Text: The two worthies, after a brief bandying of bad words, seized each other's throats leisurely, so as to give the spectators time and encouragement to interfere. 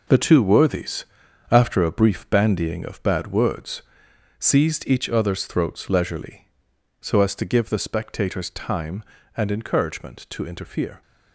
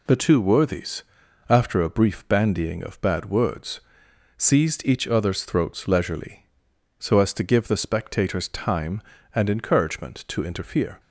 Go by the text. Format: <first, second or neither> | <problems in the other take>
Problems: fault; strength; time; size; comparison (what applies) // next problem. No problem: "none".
second | gets quieter; strong; throughout; 9 dB